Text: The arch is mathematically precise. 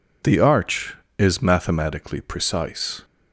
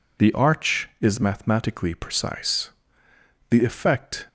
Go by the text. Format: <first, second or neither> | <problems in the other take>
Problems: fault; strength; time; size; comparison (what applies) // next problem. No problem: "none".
first | goes on to say "The effect"; noticeable; from 3.4 s on; 0.78 s long